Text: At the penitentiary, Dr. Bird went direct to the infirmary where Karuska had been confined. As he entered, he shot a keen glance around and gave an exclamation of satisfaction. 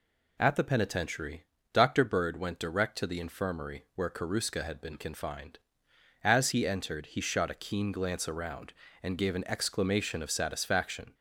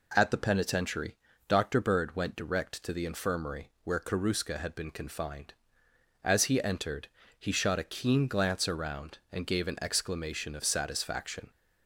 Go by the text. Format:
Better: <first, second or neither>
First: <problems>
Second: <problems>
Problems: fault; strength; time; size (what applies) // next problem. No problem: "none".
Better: neither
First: none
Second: none